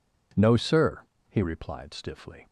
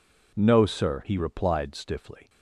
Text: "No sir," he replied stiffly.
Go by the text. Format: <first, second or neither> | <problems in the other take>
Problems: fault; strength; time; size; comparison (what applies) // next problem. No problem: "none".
neither | none